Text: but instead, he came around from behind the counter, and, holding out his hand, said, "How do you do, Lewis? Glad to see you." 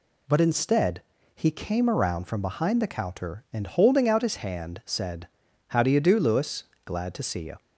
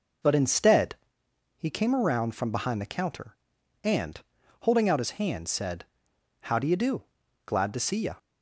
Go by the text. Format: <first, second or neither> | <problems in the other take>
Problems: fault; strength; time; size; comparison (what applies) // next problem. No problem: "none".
first | skips "Lewis"; at 7.2 s